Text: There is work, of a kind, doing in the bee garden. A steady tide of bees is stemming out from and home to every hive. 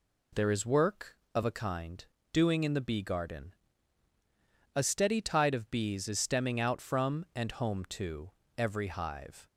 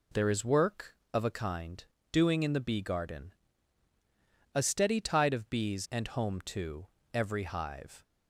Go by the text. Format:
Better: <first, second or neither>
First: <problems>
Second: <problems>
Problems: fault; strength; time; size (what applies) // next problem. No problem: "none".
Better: first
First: pauses between "to" and "every"; slight; at 8.3 s; 0.26 s long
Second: skips "is stemming out from"; at 5.8 s // pauses between "to" and "every"; slight; at 6.8 s; 0.26 s long